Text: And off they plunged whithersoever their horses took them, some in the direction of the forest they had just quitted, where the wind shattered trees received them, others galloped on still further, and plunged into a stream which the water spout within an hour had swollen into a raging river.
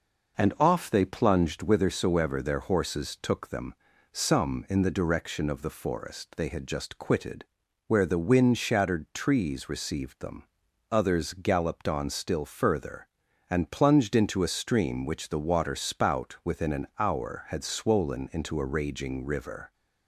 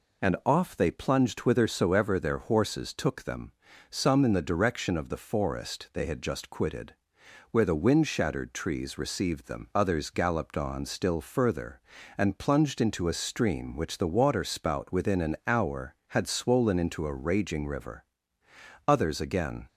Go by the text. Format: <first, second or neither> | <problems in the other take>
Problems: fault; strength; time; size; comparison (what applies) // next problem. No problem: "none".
first | goes on to say "Others again"; noticeable; from 18.8 s on; 0.80 s long